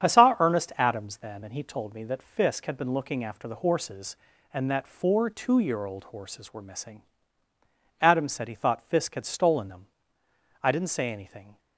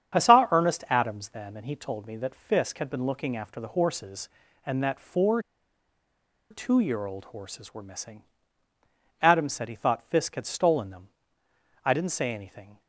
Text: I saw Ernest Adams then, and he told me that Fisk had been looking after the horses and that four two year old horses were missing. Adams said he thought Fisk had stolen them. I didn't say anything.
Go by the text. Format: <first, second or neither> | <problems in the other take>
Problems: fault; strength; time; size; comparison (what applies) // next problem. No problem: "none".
first | starts louder than the rest; strong; until 1.2 s; 8 dB; strong in the first // pauses between "four" and "two"; at 5.4 s; 1.0 s long